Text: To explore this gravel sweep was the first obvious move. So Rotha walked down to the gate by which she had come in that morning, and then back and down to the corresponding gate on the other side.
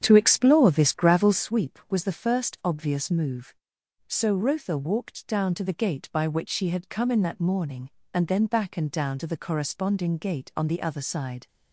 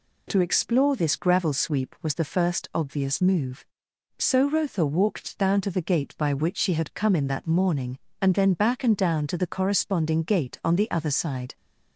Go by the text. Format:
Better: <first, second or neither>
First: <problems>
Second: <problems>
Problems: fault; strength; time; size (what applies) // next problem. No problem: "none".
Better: second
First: starts louder than the rest; strong; until 1.5 s; 8.5 dB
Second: none